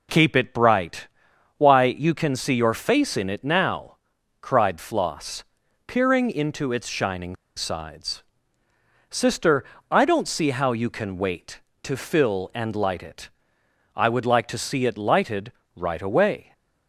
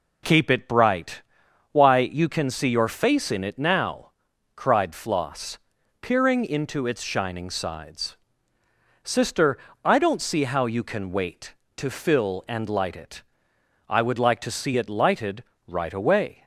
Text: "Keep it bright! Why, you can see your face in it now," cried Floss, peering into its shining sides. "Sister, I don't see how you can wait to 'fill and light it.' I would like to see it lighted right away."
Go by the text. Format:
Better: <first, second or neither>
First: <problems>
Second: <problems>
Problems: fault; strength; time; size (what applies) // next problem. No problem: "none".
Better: second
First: pauses between "shining" and "sides"; slight; at 7.3 s; 0.21 s long // pauses between "lighted" and "right"; slight; at 15.5 s; 0.24 s long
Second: pauses between "lighted" and "right"; slight; at 15.4 s; 0.24 s long